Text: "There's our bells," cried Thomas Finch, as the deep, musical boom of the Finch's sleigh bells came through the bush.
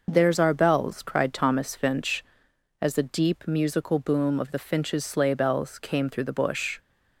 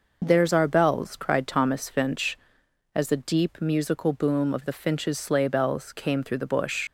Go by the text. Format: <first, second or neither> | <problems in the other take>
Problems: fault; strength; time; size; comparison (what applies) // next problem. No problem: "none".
first | leaves "bush" unfinished; at 6.8 s; 55 ms